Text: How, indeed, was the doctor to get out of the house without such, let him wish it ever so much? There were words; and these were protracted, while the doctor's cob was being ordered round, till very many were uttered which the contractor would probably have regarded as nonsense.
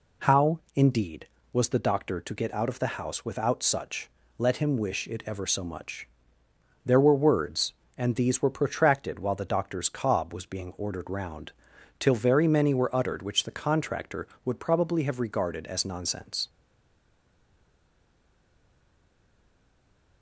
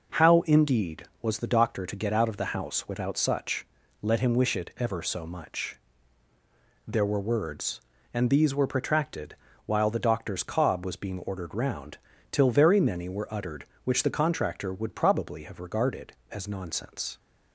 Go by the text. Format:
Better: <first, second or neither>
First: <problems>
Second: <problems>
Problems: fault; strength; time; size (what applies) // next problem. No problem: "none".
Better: second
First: stays silent after the last word; strong; from 16.4 s on; 3.8 s long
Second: none